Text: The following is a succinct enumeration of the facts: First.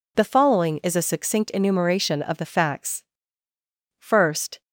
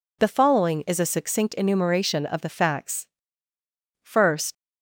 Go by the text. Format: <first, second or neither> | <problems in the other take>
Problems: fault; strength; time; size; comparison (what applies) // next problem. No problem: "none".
first | leaves "First" unfinished; at 4.5 s; 95 ms